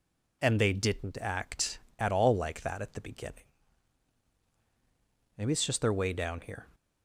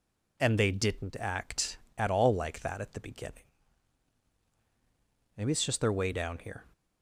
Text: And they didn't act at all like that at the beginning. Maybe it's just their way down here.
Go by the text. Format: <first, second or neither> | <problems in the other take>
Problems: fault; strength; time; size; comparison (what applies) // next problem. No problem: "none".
neither | none